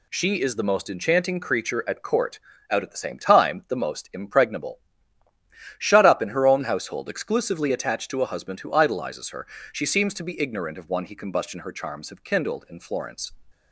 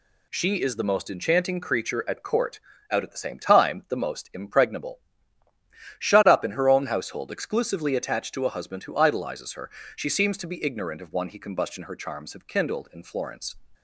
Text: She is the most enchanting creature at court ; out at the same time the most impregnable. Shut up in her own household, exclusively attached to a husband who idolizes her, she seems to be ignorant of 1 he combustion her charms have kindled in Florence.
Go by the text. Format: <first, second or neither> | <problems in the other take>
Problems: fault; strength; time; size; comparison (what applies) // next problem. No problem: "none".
neither | none